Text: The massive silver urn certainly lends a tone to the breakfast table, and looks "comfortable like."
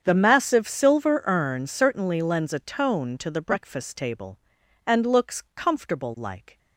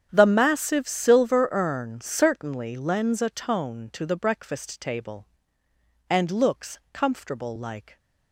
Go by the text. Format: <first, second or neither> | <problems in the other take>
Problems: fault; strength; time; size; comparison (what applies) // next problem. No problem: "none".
neither | starts louder than the rest; strong; the same in both